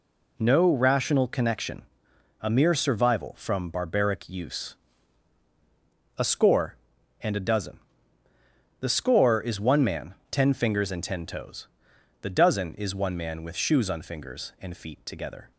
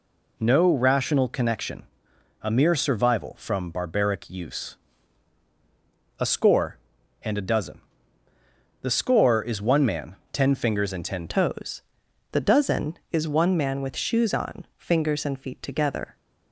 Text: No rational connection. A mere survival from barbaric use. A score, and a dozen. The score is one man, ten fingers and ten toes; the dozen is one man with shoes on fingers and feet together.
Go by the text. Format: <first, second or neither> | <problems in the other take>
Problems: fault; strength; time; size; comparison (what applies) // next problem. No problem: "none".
first | changes voice at "toes"; from 11.2 s on; 4.9 s long